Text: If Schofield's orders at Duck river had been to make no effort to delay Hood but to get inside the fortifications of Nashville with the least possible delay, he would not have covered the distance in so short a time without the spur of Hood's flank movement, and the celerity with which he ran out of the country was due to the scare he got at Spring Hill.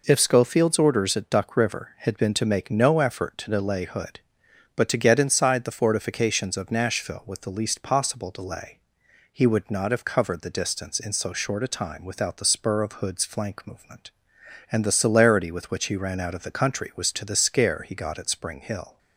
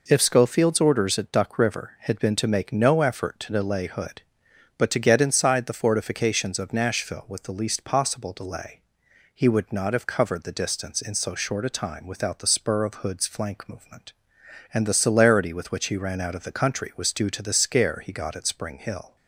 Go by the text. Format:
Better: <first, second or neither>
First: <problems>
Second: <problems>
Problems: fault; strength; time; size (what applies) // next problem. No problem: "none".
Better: second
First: skips "due"; at 17.1 s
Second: none